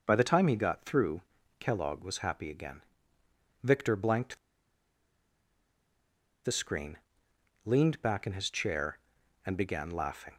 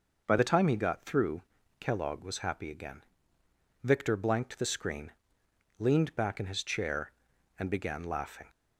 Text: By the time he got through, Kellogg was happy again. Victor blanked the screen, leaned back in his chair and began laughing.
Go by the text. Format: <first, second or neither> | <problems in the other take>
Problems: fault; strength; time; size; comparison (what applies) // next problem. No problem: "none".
second | pauses between "blanked" and "the"; strong; at 4.3 s; 2.0 s long